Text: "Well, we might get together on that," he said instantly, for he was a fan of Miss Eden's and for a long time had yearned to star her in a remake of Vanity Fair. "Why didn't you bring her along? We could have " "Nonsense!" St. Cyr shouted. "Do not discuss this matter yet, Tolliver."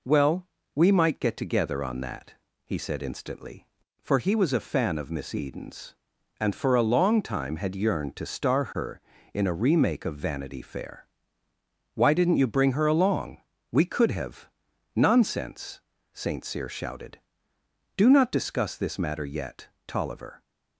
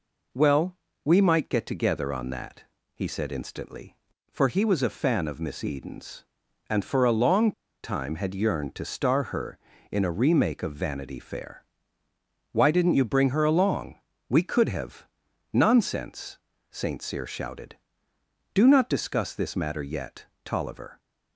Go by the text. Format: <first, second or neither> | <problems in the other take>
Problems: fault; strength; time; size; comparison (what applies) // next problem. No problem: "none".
first | pauses between "long" and "time"; slight; at 7.5 s; 0.32 s long